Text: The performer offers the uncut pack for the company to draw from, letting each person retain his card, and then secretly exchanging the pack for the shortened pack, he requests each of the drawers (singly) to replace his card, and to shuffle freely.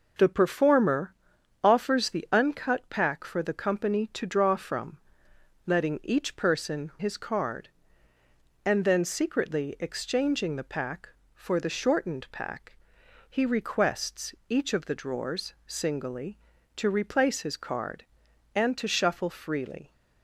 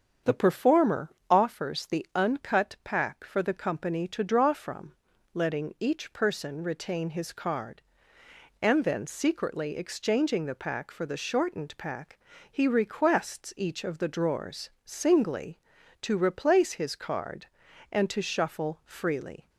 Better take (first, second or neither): second